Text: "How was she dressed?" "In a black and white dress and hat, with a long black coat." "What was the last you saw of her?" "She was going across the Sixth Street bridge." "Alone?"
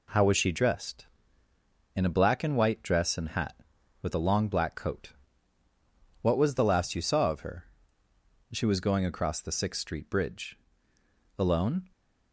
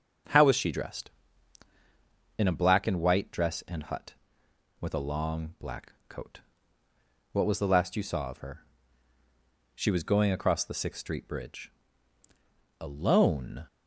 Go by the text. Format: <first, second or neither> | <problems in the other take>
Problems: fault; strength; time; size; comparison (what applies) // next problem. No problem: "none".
first | says "hut" for "hat"; at 3.8 s